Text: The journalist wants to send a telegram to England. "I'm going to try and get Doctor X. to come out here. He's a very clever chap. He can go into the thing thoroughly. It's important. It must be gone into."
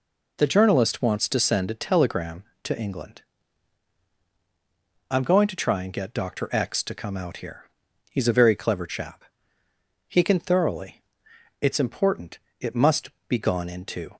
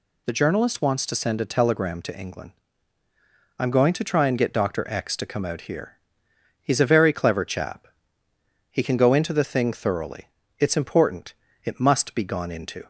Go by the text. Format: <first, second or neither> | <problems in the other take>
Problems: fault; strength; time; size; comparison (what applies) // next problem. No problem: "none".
second | skips "go into the thing"; at 10.3 s // pauses between "must" and "be"; slight; at 13.0 s; 0.18 s long